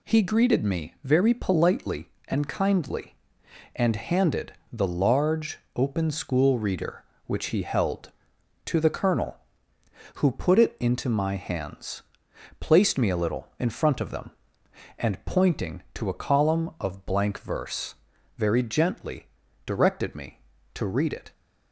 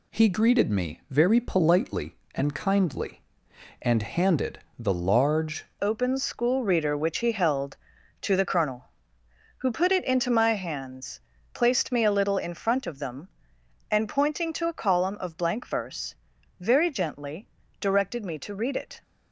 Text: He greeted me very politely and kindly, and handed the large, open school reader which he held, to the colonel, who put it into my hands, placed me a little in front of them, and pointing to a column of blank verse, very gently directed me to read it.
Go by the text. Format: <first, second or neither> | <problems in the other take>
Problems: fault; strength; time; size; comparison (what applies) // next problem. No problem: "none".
first | pauses between "handed" and "the"; slight; at 4.5 s; 0.20 s long; slight in the first // changes voice at "open"; from 5.8 s on; 13.2 s long // pauses between "gently" and "directed"; slight; at 17.4 s; 0.32 s long; also in the first